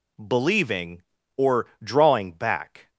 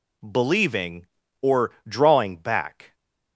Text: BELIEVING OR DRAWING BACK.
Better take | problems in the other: neither | pauses between "OR" and "DRAWING"; slight; the same in both

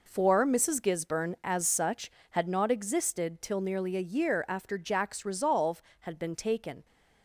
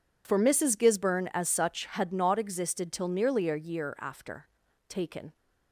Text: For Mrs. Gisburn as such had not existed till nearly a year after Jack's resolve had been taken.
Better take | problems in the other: first | skips "Jack's resolve had been"; at 4.6 s

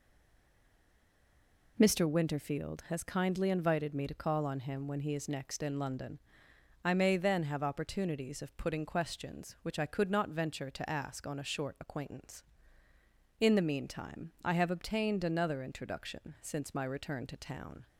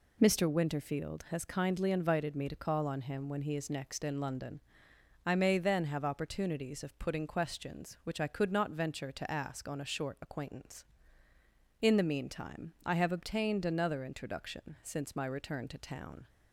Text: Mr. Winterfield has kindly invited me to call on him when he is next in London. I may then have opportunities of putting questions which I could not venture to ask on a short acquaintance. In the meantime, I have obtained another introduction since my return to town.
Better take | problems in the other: second | stays silent before the first word; noticeable; until 1.7 s; 1.7 s long

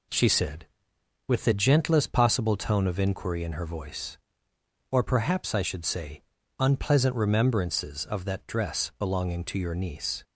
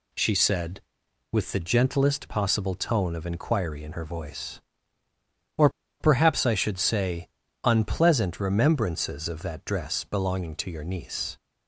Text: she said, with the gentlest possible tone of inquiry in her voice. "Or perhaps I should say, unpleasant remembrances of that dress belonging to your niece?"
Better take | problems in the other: first | pauses between "Or" and "perhaps"; slight; at 5.6 s; 0.30 s long

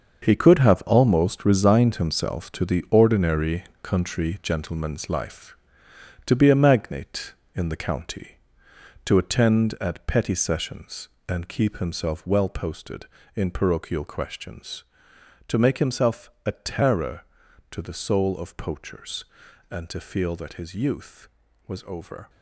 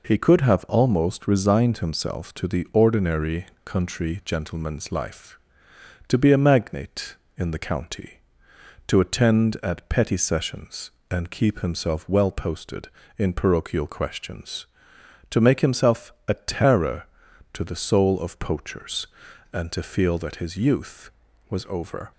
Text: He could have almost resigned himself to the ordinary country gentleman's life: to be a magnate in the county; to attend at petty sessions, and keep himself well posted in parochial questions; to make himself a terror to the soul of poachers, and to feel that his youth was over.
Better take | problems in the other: second | gets quieter; strong; throughout; 10.5 dB // pauses between "ordinary" and "country"; slight; at 3.6 s; 0.16 s long; slight in the second // pauses between "himself" and "a"; slight; at 16.2 s; 0.16 s long; slight in the second

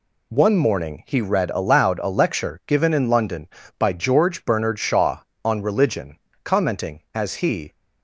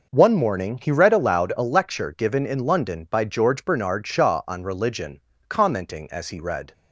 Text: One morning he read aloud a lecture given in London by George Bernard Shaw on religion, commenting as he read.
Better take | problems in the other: second | stops before "read"; at 7.7 s

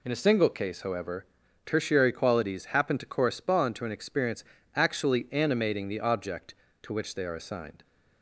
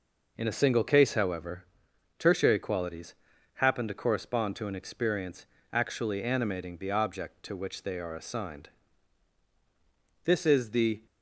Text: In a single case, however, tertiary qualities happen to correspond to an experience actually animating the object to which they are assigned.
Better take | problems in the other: first | pauses between "qualities" and "happen"; at 3.1 s; 0.42 s long // pauses between "experience" and "actually"; slight; at 5.4 s; 0.26 s long; slight in the first // goes on to say "This is the"; noticeable; from 10.2 s on; 0.82 s long

